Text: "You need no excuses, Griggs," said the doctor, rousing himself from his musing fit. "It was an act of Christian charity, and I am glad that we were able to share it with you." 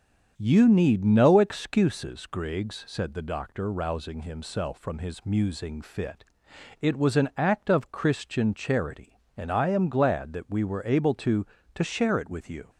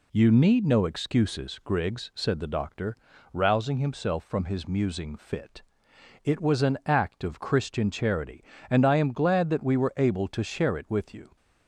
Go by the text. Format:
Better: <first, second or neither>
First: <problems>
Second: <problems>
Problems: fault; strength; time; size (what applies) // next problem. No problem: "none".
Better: second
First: starts louder than the rest; strong; until 1.3 s; 7.5 dB // says "to" twice; at 11.7 s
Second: none